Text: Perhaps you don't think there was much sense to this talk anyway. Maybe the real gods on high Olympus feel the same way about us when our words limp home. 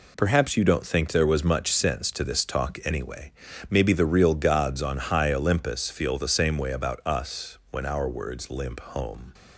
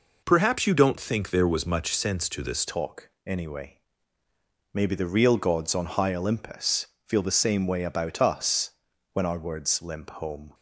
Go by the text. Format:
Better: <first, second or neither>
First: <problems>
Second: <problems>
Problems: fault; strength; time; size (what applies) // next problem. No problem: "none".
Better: first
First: none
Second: changes voice at "talk"; from 2.6 s on; 7.9 s long // pauses between "talk" and "anyway"; slight; at 3.0 s; 0.16 s long // pauses between "Olympus" and "feel"; slight; at 6.8 s; 0.20 s long // pauses between "us" and "when"; at 8.6 s; 0.42 s long